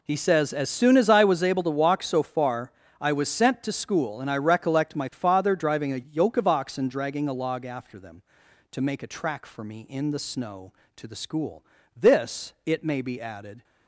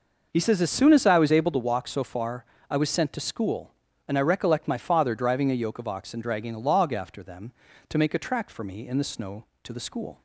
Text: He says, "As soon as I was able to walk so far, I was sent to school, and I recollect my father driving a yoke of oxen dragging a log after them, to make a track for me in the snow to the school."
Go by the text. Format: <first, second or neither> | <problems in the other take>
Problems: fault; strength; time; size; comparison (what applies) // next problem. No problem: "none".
second | goes on to say "This it may be added"; strong; from 11.9 s on; 1.6 s long